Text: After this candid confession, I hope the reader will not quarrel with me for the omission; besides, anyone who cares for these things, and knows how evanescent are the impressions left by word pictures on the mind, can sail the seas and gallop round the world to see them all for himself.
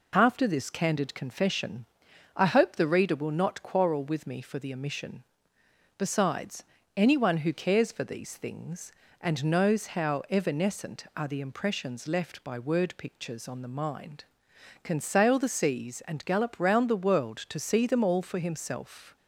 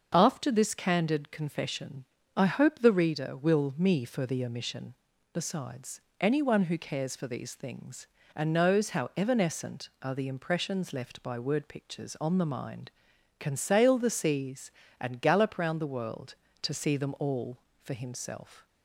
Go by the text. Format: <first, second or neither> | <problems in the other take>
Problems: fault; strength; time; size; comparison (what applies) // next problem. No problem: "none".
first | skips "not quarrel with"; at 3.7 s